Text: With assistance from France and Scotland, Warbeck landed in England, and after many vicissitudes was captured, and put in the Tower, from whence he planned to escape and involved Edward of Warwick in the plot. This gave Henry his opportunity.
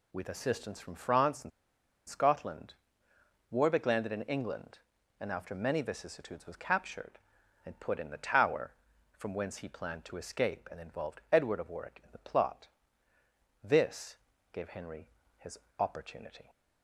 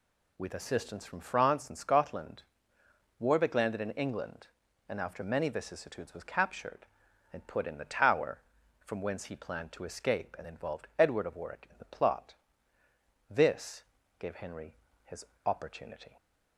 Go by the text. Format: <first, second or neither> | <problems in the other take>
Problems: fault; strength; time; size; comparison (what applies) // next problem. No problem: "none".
second | pauses between "and" and "Scotland"; noticeable; at 1.5 s; 0.59 s long // pauses between "This" and "gave"; slight; at 14.1 s; 0.34 s long; slight in the second // pauses between "Henry" and "his"; slight; at 15.0 s; 0.30 s long; slight in the second // pauses between "his" and "opportunity"; slight; at 15.5 s; 0.22 s long; slight in the second